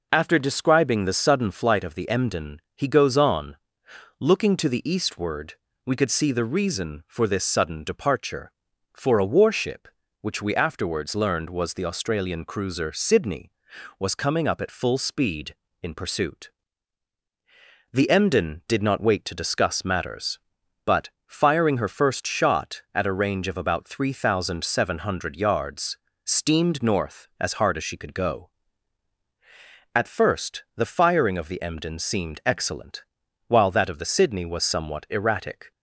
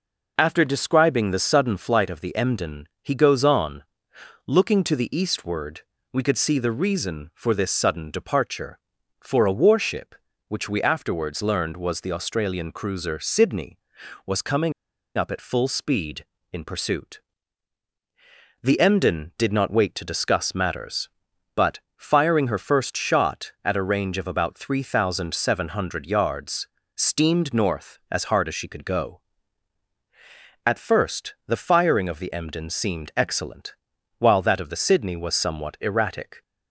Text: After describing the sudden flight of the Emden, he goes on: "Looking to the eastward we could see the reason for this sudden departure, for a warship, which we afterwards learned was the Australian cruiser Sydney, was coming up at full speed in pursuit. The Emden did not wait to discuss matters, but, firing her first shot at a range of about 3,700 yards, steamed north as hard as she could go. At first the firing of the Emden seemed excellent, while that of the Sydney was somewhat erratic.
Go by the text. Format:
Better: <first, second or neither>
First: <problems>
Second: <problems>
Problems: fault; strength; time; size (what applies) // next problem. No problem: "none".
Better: first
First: pauses between "eastward" and "we"; slight; at 5.5 s; 0.30 s long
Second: pauses between "eastward" and "we"; slight; at 5.8 s; 0.30 s long // pauses between "coming" and "up"; at 14.7 s; 0.43 s long